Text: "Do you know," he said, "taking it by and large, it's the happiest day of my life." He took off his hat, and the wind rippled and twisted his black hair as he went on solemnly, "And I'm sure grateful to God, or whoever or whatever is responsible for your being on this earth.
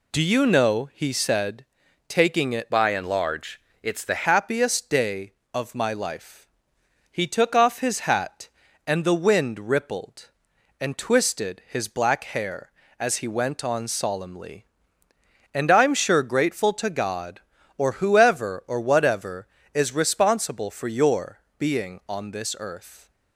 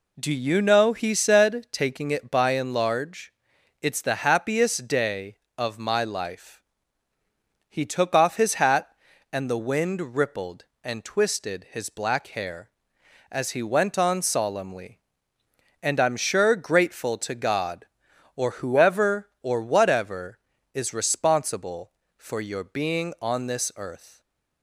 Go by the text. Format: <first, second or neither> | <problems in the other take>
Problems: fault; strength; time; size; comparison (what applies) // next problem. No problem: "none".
second | changes voice from "by" to "the"; from 2.7 to 4.2 s; 1.5 s long // pauses between "your" and "being"; slight; at 21.3 s; 0.18 s long